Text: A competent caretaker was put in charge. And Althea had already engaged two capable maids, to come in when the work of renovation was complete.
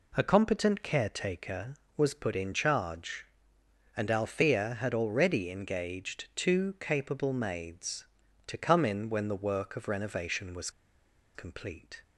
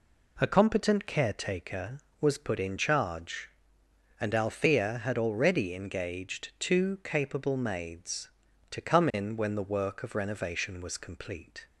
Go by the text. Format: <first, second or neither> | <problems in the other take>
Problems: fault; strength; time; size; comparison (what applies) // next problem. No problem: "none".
second | pauses between "was" and "complete"; noticeable; at 10.6 s; 0.65 s long